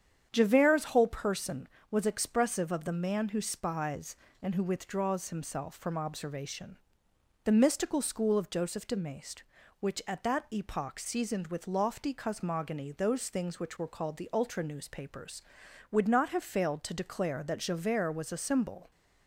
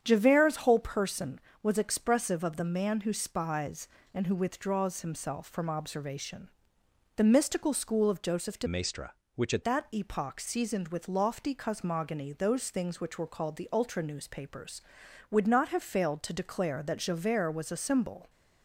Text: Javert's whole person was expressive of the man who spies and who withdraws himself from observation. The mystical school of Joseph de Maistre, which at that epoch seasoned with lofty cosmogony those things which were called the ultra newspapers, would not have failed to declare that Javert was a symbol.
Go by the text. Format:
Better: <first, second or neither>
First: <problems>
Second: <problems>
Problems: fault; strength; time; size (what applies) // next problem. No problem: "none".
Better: first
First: starts louder than the rest; strong; until 1.3 s; 8.5 dB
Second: starts louder than the rest; strong; until 1.0 s; 8.5 dB // changes voice from "Maistre" to "at"; from 8.6 to 9.6 s; 1.0 s long